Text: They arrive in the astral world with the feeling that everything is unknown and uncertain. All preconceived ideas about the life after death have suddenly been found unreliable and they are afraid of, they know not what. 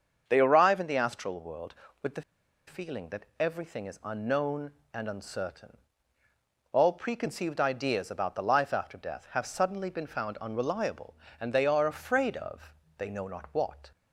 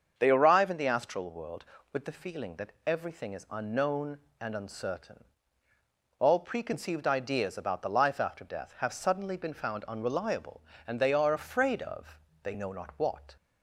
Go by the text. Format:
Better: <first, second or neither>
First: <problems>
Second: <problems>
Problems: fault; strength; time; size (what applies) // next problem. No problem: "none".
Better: second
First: starts louder than the rest; until 1.2 s; 7 dB // pauses between "the" and "feeling"; at 2.2 s; 0.45 s long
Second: starts louder than the rest; until 1.1 s; 7 dB